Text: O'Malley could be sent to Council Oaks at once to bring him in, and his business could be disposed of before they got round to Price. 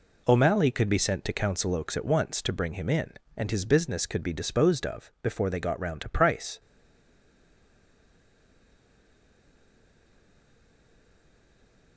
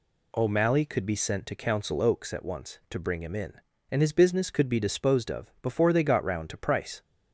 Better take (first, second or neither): second